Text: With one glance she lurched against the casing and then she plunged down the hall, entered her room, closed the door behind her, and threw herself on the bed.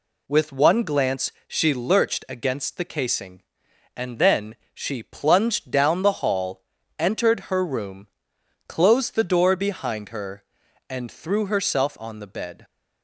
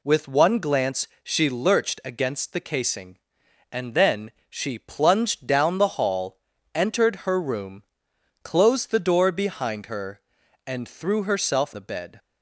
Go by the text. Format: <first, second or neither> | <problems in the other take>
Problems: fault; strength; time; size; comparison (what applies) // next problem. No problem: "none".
first | pauses between "glance" and "she"; slight; at 1.0 s; 0.16 s long; slight in the first // pauses between "then" and "she"; slight; at 4.3 s; 0.18 s long; slight in the first // skips "on"; at 11.7 s